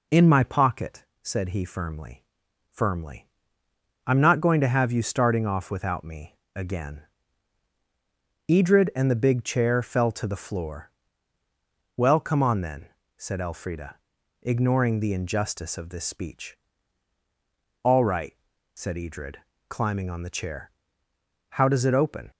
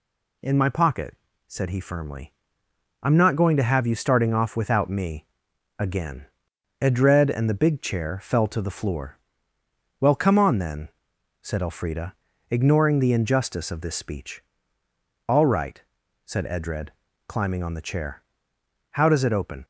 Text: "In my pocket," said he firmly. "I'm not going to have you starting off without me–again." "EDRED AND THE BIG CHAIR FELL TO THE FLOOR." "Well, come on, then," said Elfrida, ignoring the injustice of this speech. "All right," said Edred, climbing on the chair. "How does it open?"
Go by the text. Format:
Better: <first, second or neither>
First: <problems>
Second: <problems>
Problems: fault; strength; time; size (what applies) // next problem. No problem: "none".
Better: second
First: says "firmly" twice; at 2.7 s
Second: none